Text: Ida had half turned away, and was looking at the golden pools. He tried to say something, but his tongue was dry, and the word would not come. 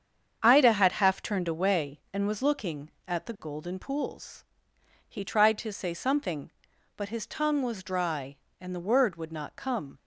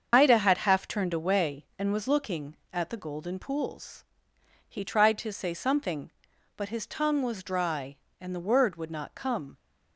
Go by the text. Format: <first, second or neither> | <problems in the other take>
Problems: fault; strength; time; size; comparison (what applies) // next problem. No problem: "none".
first | loses the start of "Ida"; at 0.1 s; 55 ms // starts louder than the rest; until 1.1 s; 7 dB; strong in the first